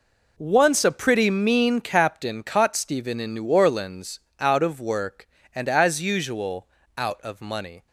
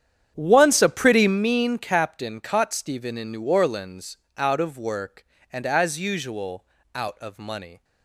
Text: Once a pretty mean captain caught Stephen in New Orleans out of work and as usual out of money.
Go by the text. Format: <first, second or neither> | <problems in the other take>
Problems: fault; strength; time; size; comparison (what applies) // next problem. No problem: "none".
first | starts louder than the rest; strong; until 1.4 s; 9 dB // pauses between "Orleans" and "out"; slight; at 4.1 s; 0.18 s long; slight in the first // pauses between "usual" and "out"; slight; at 6.6 s; 0.32 s long; slight in the first